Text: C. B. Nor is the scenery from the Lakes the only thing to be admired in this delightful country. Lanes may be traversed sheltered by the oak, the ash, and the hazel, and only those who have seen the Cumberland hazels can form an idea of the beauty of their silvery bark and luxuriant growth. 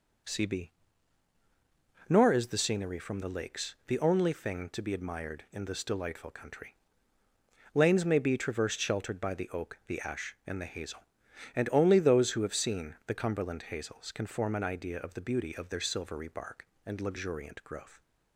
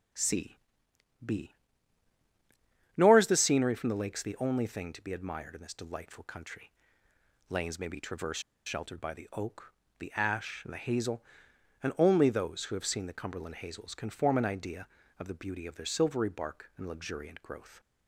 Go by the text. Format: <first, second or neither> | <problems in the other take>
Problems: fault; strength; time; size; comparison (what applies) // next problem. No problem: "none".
first | starts louder than the rest; strong; until 3.2 s; 9.5 dB // pauses between "C" and "B"; noticeable; at 0.5 s; 0.68 s long // pauses between "B" and "Nor"; strong; at 1.5 s; 1.4 s long; strong in the first // pauses between "traversed" and "sheltered"; slight; at 8.4 s; 0.24 s long